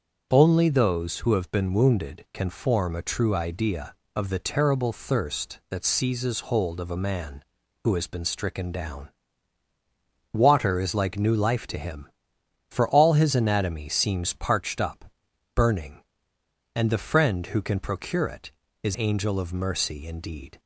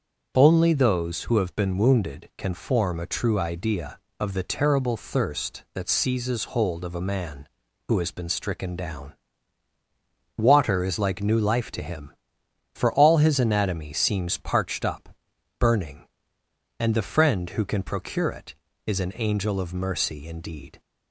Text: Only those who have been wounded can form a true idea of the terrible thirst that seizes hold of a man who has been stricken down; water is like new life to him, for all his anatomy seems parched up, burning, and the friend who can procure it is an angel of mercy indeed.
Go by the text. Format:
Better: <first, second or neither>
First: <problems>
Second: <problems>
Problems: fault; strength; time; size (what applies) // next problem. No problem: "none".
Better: second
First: starts louder than the rest; until 1.3 s; 7 dB // skips "an"; at 18.9 s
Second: starts louder than the rest; until 1.3 s; 7 dB